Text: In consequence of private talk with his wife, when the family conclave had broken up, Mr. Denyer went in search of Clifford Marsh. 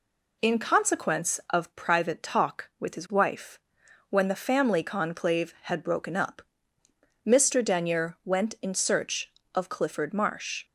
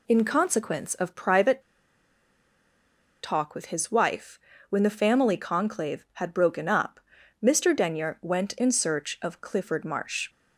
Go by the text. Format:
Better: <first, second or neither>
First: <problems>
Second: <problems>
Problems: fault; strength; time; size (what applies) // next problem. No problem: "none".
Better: first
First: none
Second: pauses between "private" and "talk"; strong; at 1.6 s; 1.6 s long